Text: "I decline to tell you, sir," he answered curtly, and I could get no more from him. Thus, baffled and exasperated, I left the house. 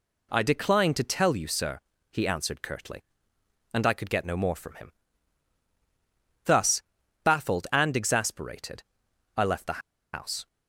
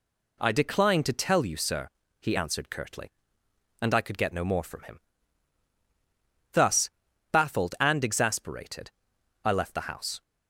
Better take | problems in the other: second | pauses between "the" and "house"; slight; at 9.8 s; 0.32 s long

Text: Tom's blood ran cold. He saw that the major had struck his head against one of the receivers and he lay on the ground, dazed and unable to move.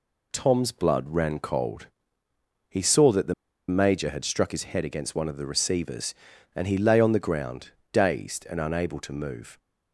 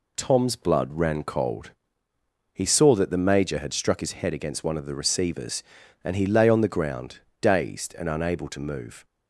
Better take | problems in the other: second | pauses between "the" and "major"; slight; at 3.3 s; 0.35 s long

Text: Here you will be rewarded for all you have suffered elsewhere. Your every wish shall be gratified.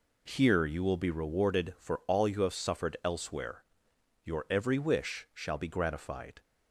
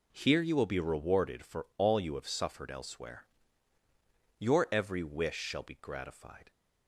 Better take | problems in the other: neither | none

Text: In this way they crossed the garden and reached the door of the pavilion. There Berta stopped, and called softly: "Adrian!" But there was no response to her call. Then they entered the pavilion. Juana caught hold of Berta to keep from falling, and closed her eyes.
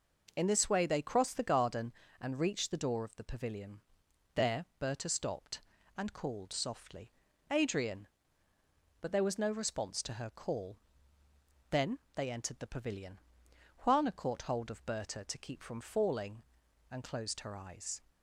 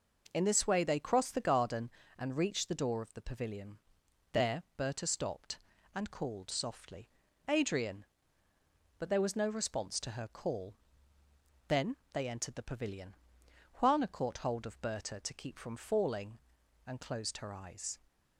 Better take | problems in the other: neither | pauses between "Then" and "they"; slight; the same in both

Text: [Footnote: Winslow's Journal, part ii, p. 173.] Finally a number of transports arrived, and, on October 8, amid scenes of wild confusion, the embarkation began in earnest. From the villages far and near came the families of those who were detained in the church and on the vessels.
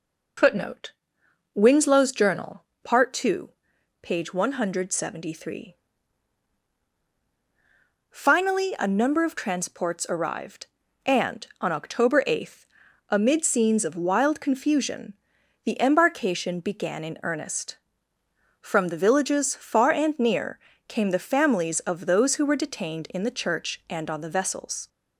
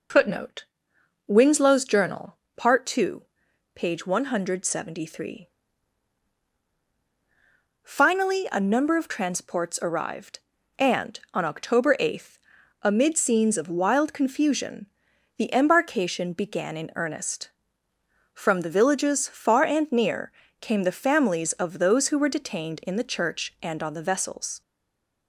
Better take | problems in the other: first | pauses between "near" and "came"; slight; at 20.3 s; 0.26 s long; slight in the first // stays silent after the last word; slight; from 24.6 s on; 0.6 s long

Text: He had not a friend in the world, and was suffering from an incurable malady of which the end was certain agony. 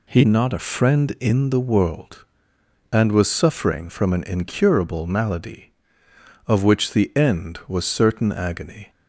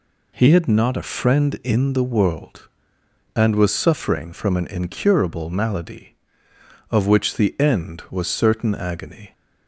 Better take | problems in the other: second | skips "had"; at 0.2 s

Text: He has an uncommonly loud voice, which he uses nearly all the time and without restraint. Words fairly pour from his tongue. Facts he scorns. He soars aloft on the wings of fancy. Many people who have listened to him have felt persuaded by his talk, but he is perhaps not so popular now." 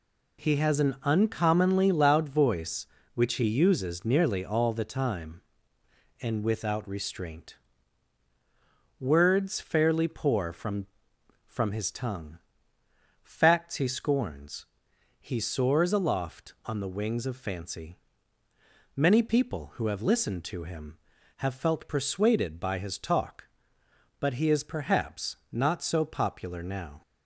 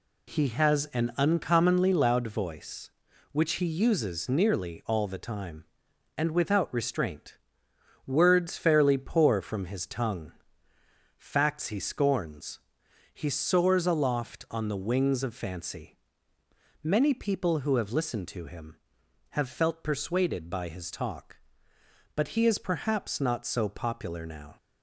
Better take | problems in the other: second | says "from" twice; at 11.4 s // pauses between "perhaps" and "not"; slight; at 25.3 s; 0.16 s long

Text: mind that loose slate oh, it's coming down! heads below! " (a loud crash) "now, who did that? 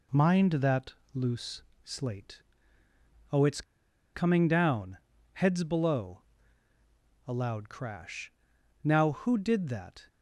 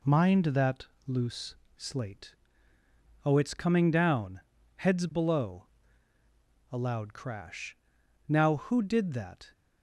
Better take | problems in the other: second | pauses between "that" and "loose"; slight; at 0.9 s; 0.22 s long; slight in the second // pauses between "loose" and "slate"; slight; at 1.6 s; 0.22 s long; slight in the second // pauses between "slate" and "oh"; noticeable; at 2.3 s; 0.92 s long; noticeable in the second // pauses between "it's" and "coming"; noticeable; at 3.6 s; 0.52 s long

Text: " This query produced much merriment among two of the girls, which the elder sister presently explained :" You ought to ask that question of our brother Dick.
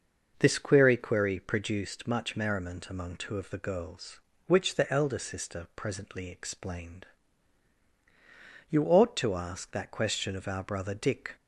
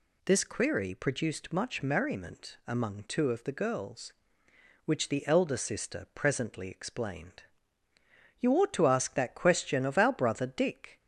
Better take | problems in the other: second | starts louder than the rest; until 1.3 s; 6.5 dB // says "query" twice; at 0.9 s

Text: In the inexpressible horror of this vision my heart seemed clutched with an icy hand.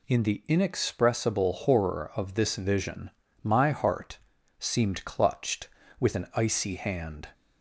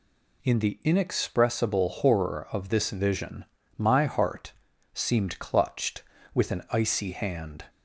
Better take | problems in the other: neither | pauses between "vision" and "my"; slight; the same in both // pauses between "heart" and "seemed"; the same in both

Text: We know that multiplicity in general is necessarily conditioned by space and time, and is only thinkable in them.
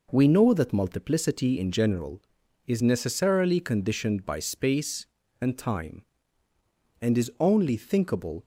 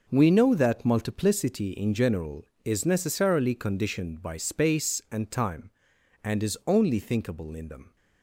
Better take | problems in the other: second | stops before "in them"; at 8.4 s

